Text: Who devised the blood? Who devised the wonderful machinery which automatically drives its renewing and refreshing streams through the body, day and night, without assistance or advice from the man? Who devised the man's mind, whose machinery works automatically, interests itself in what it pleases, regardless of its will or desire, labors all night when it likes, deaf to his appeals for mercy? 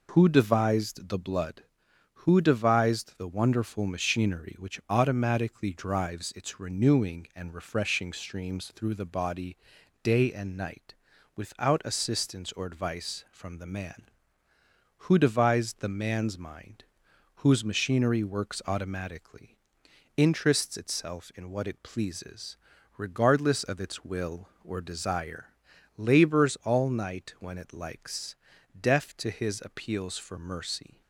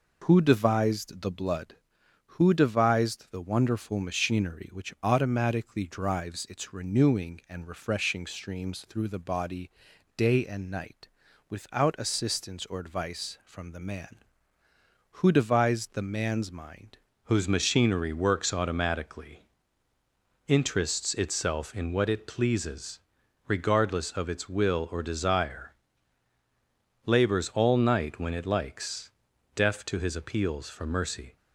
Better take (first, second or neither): first